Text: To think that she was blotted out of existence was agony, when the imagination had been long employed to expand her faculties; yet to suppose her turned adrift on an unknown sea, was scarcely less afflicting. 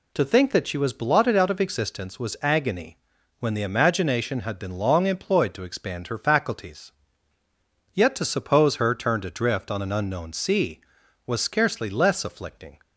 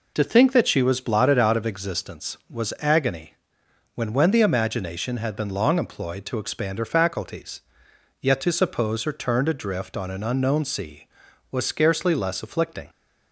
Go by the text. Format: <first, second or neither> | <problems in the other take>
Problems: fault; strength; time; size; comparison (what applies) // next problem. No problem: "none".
first | says "when" twice; at 4.1 s